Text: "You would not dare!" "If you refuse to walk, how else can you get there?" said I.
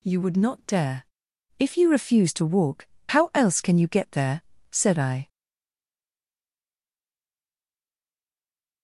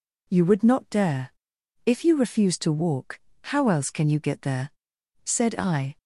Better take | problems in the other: second | stays silent after the last word; strong; from 5.2 s on; 3.6 s long

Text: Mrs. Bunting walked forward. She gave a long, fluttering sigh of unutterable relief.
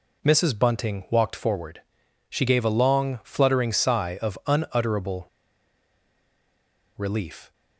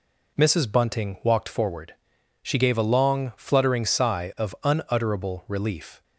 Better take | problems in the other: second | pauses between "unutterable" and "relief"; strong; at 5.2 s; 1.6 s long

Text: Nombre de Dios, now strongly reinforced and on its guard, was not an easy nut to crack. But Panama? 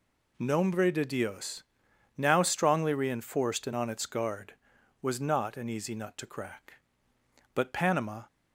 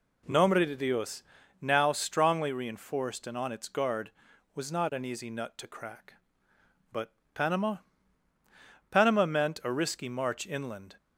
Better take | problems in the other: first | pauses between "But" and "Panama"; slight; at 7.1 s; 0.20 s long // goes on to say "Panama meant a risky march inland"; strong; from 8.9 s on; 2.0 s long

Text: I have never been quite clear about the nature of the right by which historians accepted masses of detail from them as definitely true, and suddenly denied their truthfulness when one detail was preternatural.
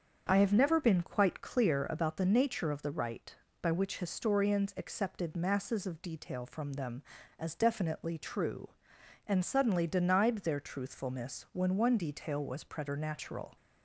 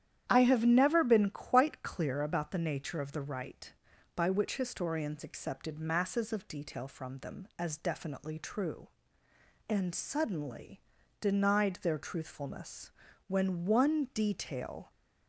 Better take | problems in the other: first | starts louder than the rest; strong; until 1.2 s; 10.5 dB; also in the first // pauses between "suddenly" and "denied"; at 10.7 s; 0.40 s long // pauses between "truthfulness" and "when"; at 12.8 s; 0.38 s long // stops before "was preternatural"; at 14.8 s

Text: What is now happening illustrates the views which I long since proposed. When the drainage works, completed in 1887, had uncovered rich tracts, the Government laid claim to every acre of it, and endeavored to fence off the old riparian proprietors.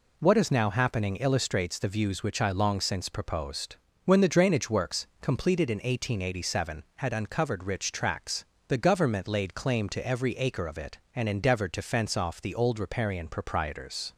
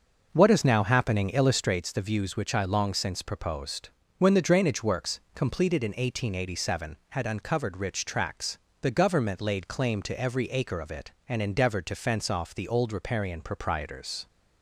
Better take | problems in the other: first | starts louder than the rest; noticeable; until 1.9 s; 6 dB

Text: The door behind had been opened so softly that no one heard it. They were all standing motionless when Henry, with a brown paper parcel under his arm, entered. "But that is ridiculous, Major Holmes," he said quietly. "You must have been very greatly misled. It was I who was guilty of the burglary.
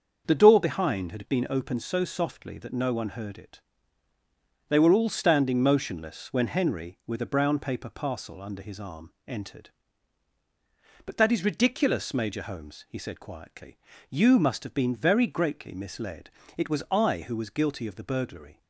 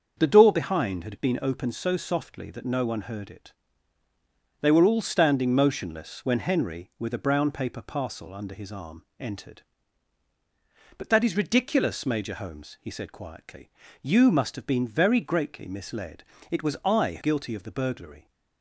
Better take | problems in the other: first | starts louder than the rest; until 1.1 s; 6.5 dB; also in the first // skips "who was"; at 17.1 s

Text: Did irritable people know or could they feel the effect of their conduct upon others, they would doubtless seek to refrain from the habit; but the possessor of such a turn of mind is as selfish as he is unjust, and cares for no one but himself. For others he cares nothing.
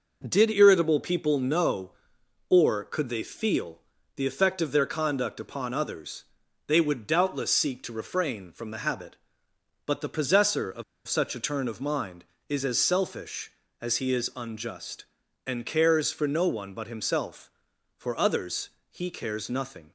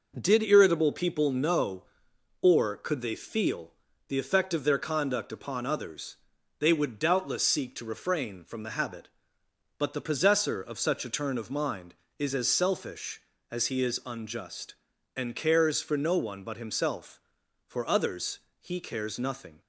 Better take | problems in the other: second | pauses between "feel" and "the"; slight; at 3.7 s; 0.36 s long; slight in the second // pauses between "of" and "such"; slight; at 10.8 s; 0.24 s long // pauses between "others" and "he"; slight; at 18.6 s; 0.22 s long; slight in the second

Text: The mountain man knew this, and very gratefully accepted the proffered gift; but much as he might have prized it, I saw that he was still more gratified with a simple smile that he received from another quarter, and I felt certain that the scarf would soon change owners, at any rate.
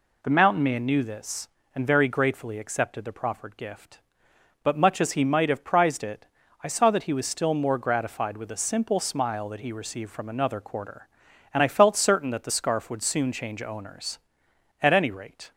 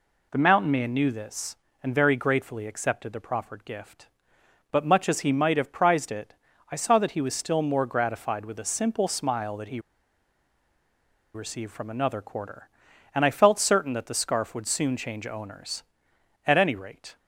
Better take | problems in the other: first | pauses between "he" and "received"; strong; at 9.7 s; 1.5 s long

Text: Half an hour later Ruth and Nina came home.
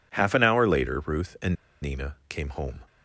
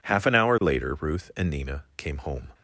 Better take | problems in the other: second | pauses between "and" and "Nina"; slight; at 1.5 s; 0.26 s long

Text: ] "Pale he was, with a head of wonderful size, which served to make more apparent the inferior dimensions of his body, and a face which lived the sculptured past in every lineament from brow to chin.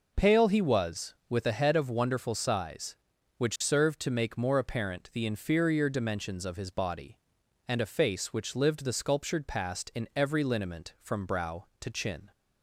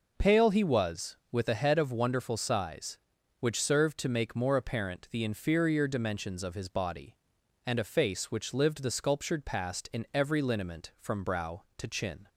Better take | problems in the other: neither | none

